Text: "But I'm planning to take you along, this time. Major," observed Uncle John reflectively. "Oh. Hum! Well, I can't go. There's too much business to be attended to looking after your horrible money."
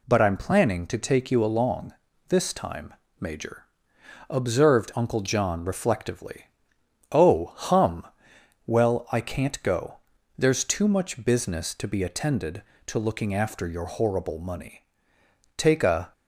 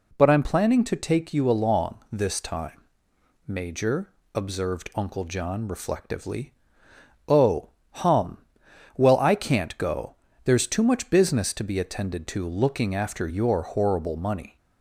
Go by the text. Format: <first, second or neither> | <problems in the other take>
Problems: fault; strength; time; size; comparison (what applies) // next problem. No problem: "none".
second | goes on to say "Take a"; from 15.5 s on; 0.54 s long